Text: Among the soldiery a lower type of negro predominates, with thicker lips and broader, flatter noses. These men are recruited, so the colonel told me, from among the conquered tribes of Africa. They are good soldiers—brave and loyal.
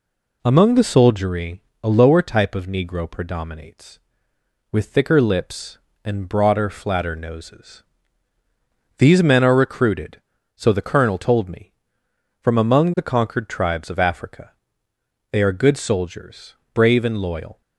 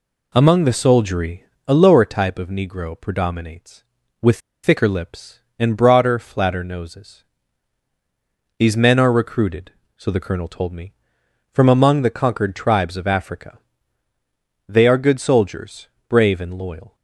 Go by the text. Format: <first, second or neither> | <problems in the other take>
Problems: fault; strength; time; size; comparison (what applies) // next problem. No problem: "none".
first | pauses between "soldiery" and "a"; slight; at 1.4 s; 0.24 s long; slight in the first // pauses between "with" and "thicker"; slight; at 4.3 s; 0.25 s long